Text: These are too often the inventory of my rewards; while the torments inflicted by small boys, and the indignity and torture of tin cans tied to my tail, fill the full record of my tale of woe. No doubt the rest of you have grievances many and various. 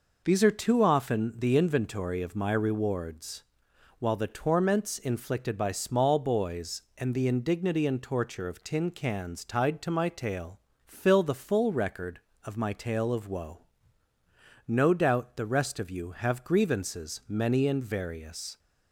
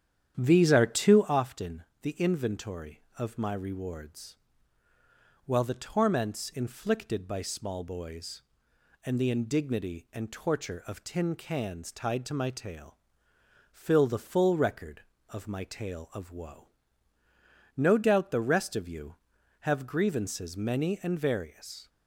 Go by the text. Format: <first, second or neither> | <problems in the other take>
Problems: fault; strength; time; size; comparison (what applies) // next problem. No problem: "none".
first | starts louder than the rest; strong; until 1.4 s; 9.5 dB // pauses between "often" and "the"; slight; at 1.8 s; 0.18 s long